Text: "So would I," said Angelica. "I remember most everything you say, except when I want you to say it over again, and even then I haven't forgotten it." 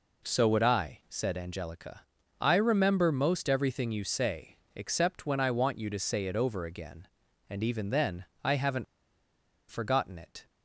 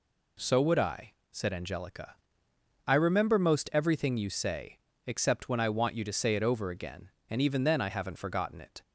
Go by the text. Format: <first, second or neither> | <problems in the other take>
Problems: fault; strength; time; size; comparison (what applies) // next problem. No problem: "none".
second | pauses between "then" and "I"; slight; at 8.2 s; 0.18 s long // pauses between "haven't" and "forgotten"; noticeable; at 8.8 s; 0.86 s long